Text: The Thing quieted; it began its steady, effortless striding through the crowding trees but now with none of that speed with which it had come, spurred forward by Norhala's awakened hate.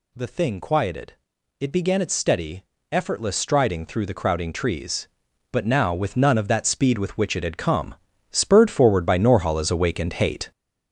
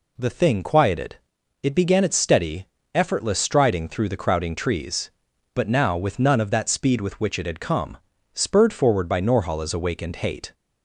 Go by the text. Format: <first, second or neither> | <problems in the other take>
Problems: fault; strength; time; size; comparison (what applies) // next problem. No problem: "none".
second | gets louder; throughout; 7 dB